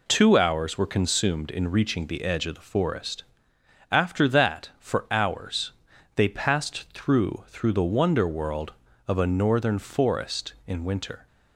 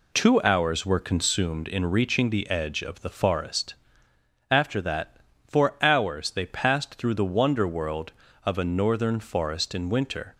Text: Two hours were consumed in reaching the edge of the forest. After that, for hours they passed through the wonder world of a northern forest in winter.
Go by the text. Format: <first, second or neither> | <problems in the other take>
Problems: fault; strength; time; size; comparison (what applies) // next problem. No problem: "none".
second | pauses between "hours" and "they"; at 5.7 s; 0.42 s long // says "through" twice; at 7.4 s